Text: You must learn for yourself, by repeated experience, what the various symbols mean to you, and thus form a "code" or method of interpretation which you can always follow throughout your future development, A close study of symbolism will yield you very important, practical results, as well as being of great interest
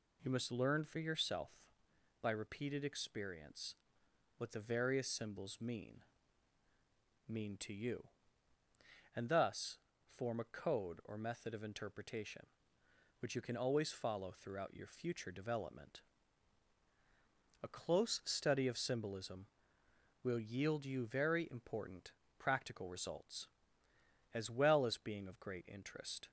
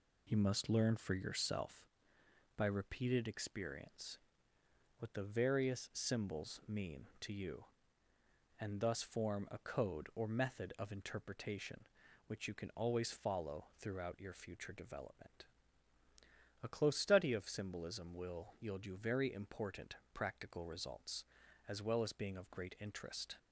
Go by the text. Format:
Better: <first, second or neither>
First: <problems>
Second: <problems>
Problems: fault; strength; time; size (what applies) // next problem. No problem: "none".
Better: second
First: says "mean" twice; at 7.2 s // pauses between "thus" and "form"; slight; at 9.7 s; 0.26 s long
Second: none